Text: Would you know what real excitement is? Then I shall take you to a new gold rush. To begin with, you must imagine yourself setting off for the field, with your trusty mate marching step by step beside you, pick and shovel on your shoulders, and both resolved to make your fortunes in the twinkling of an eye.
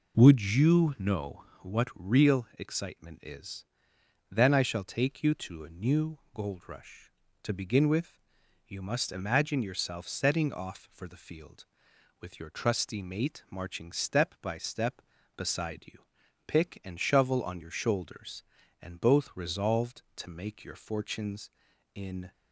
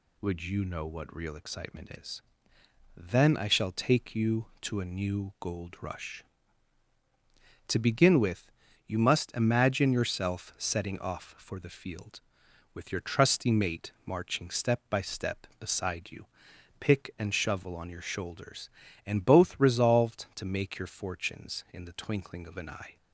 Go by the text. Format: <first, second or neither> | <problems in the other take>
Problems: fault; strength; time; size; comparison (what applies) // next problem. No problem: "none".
second | pauses between "know" and "what"; slight; at 1.4 s; 0.18 s long // pauses between "new" and "gold"; slight; at 6.1 s; 0.16 s long // stops before "the twinkling of an eye"; at 22.3 s